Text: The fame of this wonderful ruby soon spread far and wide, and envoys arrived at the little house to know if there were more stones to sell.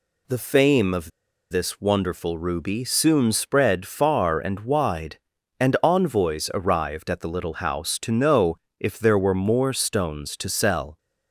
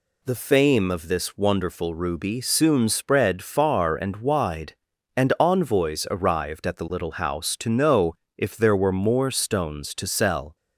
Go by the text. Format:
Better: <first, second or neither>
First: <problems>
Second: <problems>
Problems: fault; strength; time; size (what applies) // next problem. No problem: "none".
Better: second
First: pauses between "of" and "this"; at 1.1 s; 0.41 s long // pauses between "know" and "if"; slight; at 8.5 s; 0.24 s long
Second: pauses between "know" and "if"; slight; at 8.1 s; 0.24 s long